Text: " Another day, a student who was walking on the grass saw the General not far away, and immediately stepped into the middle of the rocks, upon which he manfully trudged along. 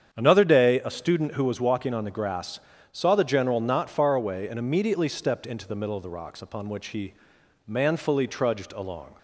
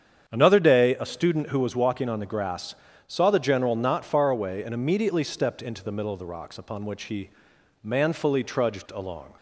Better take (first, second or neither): neither